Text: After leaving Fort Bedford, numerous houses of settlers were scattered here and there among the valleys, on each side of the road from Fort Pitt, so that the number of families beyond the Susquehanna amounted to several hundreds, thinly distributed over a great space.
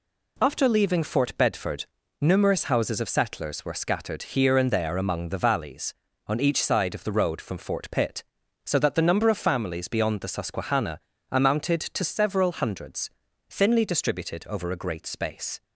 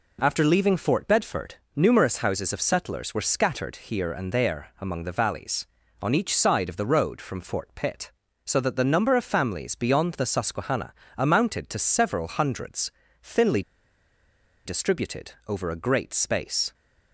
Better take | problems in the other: first | pauses between "Susquehanna" and "amounted"; slight; at 10.9 s; 0.24 s long; slight in the first // pauses between "thinly" and "distributed"; at 13.6 s; 1.0 s long

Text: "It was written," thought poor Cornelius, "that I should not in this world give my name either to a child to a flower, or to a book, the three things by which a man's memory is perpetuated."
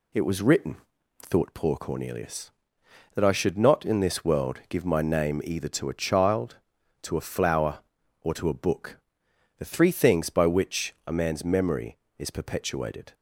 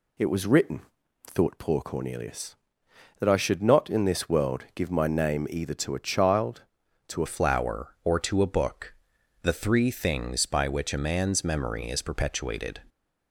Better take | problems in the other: first | changes voice at "flower"; from 7.2 s on; 5.5 s long

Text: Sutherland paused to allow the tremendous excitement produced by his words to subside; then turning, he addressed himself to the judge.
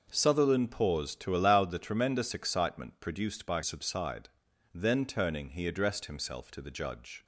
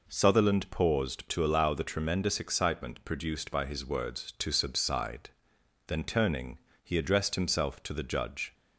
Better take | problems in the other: second | starts louder than the rest; noticeable; until 1.1 s; 6 dB // skips "his words to"; at 3.6 s

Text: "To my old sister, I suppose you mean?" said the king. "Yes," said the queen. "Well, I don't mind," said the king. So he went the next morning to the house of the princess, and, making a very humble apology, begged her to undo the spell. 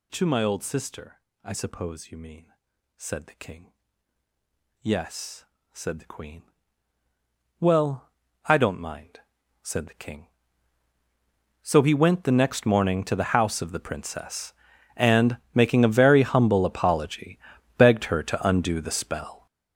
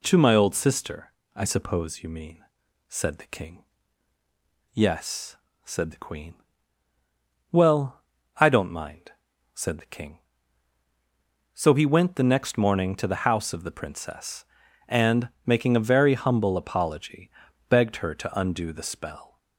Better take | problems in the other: second | gets louder; strong; throughout; 13 dB

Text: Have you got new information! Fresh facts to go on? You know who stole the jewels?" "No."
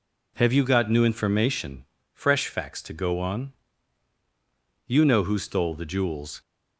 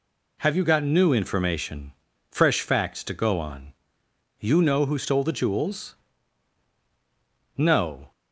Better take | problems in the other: second | stops before "No"; at 6.4 s

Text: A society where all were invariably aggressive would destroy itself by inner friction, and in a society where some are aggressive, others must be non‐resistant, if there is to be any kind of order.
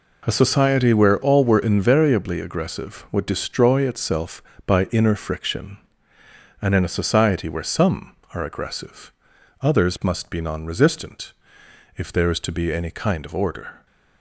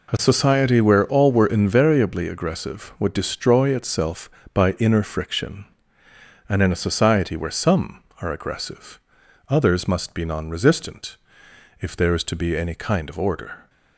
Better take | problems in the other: neither | none

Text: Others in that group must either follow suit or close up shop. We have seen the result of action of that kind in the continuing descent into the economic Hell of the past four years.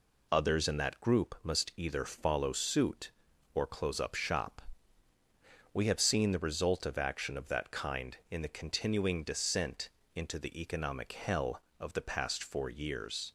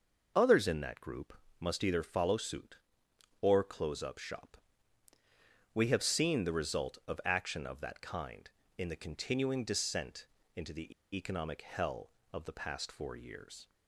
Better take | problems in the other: first | pauses between "group" and "must"; slight; at 1.3 s; 0.26 s long // pauses between "descent" and "into"; slight; at 10.2 s; 0.28 s long; slight in the first // pauses between "the" and "economic"; slight; at 10.9 s; 0.22 s long

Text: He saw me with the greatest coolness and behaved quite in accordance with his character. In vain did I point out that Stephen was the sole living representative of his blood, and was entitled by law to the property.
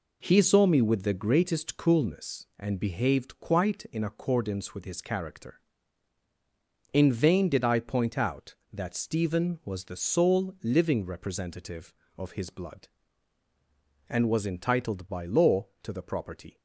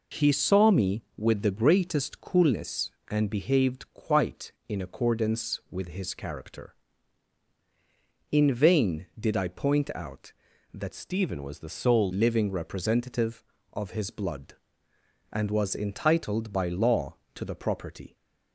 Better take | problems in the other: first | changes voice from "Stephen" to "sole"; from 10.9 to 12.1 s; 1.2 s long

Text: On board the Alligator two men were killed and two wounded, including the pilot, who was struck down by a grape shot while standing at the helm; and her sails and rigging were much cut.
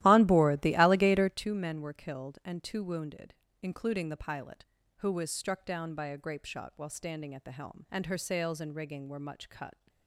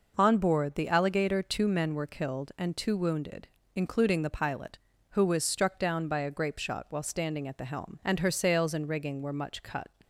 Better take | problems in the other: second | starts louder than the rest; strong; until 1.4 s; 14.5 dB

